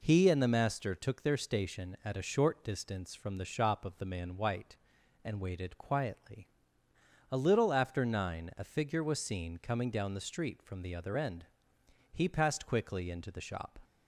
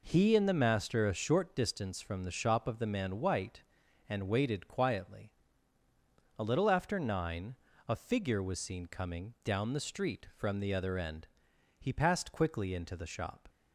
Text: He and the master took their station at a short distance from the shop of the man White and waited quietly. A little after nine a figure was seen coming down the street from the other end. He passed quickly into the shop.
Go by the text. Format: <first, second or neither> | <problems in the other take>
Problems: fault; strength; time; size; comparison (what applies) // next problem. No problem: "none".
first | skips "took their station at"; at 1.0 s // pauses between "nine" and "a"; slight; at 7.5 s; 0.34 s long